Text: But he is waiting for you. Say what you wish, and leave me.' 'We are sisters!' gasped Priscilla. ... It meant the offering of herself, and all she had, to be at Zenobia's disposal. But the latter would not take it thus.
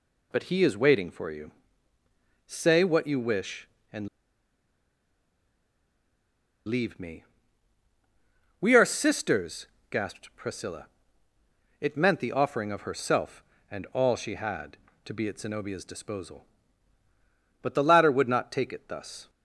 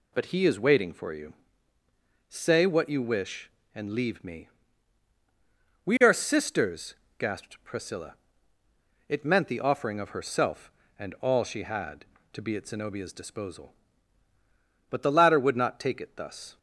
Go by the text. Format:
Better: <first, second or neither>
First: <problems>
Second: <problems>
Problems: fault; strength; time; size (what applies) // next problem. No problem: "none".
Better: second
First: pauses between "and" and "leave"; strong; at 4.0 s; 2.5 s long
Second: none